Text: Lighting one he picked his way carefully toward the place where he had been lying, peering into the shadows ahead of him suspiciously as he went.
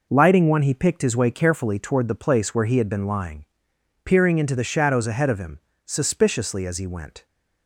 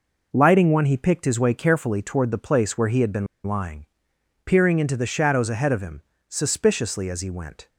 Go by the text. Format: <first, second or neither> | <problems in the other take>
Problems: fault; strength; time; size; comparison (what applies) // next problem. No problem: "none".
first | pauses between "been" and "lying"; slight; at 3.2 s; 0.20 s long // pauses between "him" and "suspiciously"; slight; at 6.0 s; 0.30 s long; slight in the first